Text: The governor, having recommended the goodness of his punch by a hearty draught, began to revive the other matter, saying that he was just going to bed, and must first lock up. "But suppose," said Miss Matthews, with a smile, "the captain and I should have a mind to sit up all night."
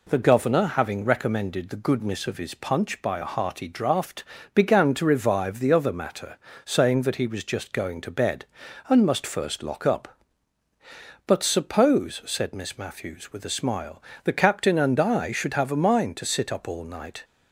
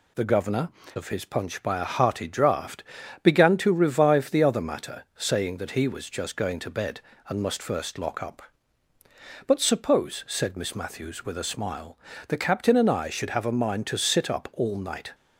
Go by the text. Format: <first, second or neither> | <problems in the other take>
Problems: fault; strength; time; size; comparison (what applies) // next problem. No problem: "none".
first | skips "having recommended the goodness"; at 0.8 s